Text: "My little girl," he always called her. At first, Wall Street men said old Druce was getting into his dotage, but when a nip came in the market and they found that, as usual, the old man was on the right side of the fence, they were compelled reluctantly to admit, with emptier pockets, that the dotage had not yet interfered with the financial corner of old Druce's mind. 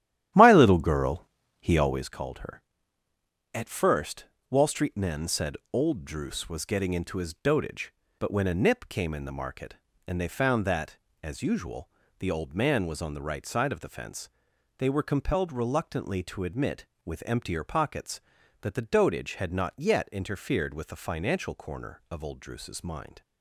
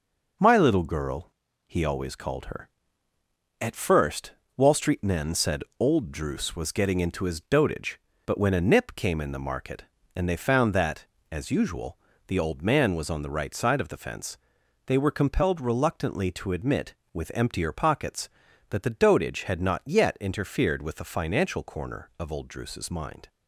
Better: second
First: starts louder than the rest; strong; until 2.2 s; 12 dB // pauses between "said" and "old"; slight; at 5.5 s; 0.16 s long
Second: pauses between "said" and "old"; slight; at 5.6 s; 0.16 s long

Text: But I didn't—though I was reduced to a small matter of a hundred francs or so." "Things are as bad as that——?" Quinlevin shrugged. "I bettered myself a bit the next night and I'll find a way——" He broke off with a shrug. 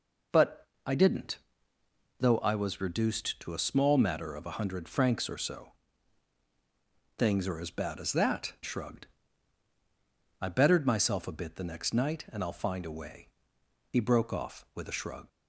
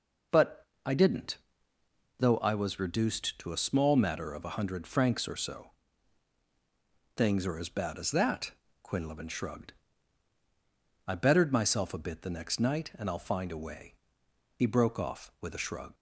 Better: second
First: pauses between "But" and "I"; slight; at 0.6 s; 0.18 s long // skips "Quinlevin"; at 8.5 s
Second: pauses between "But" and "I"; slight; at 0.6 s; 0.18 s long

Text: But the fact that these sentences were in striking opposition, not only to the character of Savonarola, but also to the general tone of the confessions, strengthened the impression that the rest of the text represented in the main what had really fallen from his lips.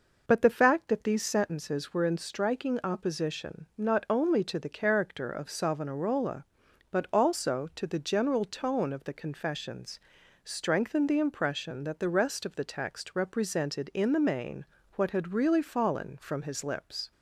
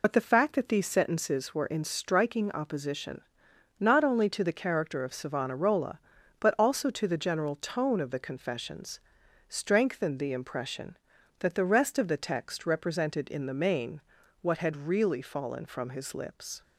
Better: first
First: pauses between "main" and "what"; slight; at 14.6 s; 0.30 s long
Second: loses the start of "But"; at 0.0 s; 55 ms // pauses between "main" and "what"; at 14.0 s; 0.42 s long

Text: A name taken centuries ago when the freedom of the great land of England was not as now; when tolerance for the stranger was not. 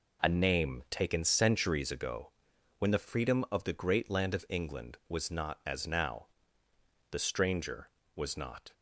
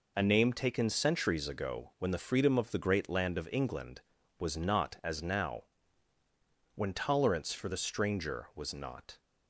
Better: second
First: pauses between "ago" and "when"; noticeable; at 2.3 s; 0.46 s long // skips "when tolerance for"; at 6.6 s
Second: none

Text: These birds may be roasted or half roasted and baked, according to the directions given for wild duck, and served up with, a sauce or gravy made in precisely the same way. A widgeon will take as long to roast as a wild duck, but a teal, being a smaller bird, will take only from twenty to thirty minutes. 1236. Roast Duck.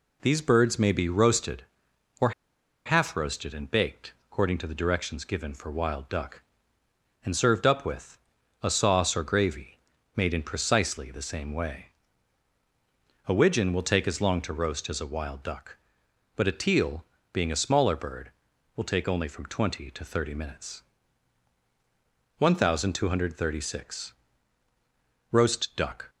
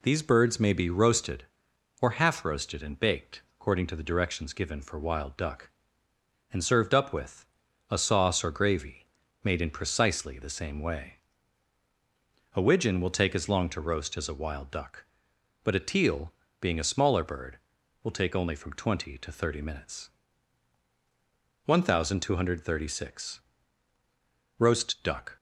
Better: second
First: pauses between "or" and "half"; noticeable; at 2.3 s; 0.54 s long // pauses between "gravy" and "made"; at 9.7 s; 0.38 s long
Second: pauses between "gravy" and "made"; at 9.0 s; 0.38 s long

